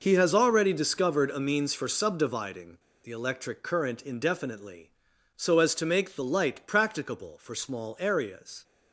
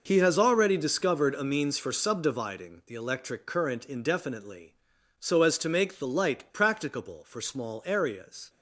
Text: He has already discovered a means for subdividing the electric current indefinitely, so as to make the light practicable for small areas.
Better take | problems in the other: second | pauses between "subdividing" and "the"; slight; at 2.7 s; 0.24 s long

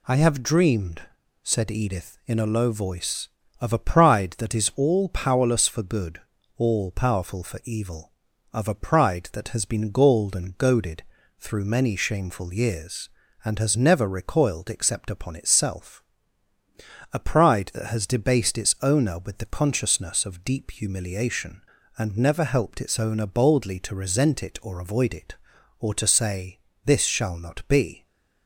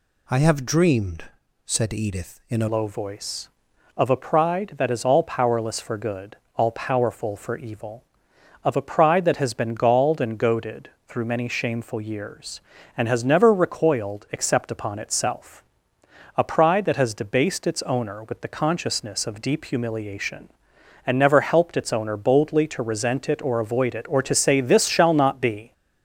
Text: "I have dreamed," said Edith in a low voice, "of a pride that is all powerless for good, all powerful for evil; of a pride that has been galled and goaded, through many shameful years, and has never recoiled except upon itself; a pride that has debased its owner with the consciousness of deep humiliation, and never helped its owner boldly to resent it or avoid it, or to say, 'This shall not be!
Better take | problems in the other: first | changes voice at "low"; from 2.6 s on; 23.1 s long

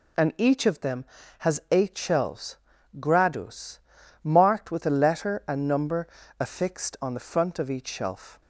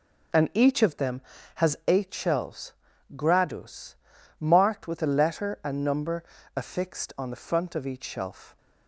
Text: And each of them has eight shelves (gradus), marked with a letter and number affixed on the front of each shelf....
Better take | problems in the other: first | starts louder than the rest; noticeable; until 2.0 s; 5.5 dB // pauses between "number" and "affixed"; slight; at 6.2 s; 0.32 s long; slight in the first

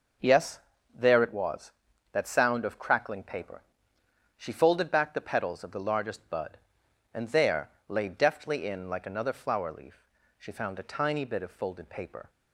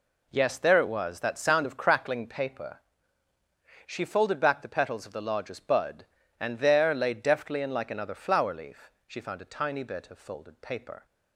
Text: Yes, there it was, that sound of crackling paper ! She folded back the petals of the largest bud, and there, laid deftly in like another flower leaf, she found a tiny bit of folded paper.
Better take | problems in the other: neither | none

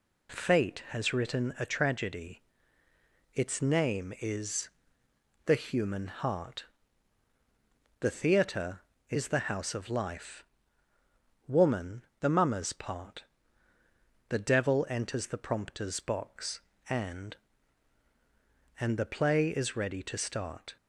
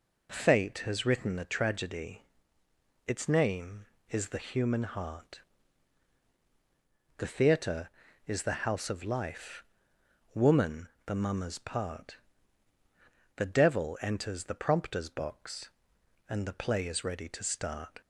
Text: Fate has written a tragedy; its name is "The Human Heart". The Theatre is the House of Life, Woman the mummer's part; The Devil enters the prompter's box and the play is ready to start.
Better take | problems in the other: second | pauses between "is" and "The"; noticeable; at 4.6 s; 0.78 s long // pauses between "Woman" and "the"; slight; at 12.0 s; 0.16 s long; slight in the second // says "and" twice; at 18.7 s

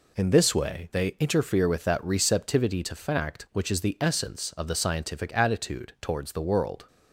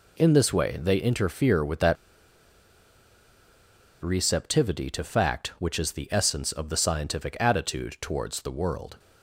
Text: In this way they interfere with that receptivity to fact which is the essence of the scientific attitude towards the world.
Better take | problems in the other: first | pauses between "that" and "receptivity"; strong; at 1.9 s; 2.0 s long

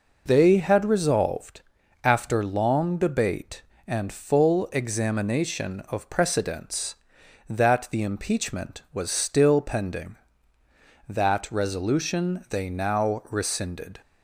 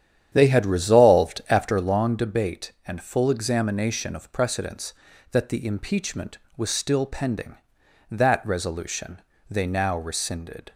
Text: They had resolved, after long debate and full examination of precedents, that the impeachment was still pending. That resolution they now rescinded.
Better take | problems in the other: first | starts louder than the rest; strong; until 2.0 s; 9.5 dB // pauses between "resolution" and "they"; slight; at 9.2 s; 0.28 s long

